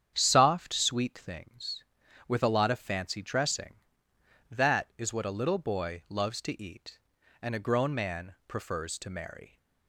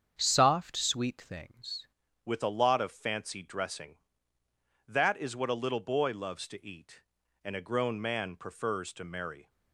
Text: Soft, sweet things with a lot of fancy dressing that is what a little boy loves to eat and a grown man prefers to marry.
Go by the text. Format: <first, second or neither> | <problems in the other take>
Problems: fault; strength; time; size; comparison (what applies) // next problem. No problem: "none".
first | starts louder than the rest; strong; until 1.2 s; 7.5 dB; strong in the first // changes voice at "with"; from 2.2 s on; 7.2 s long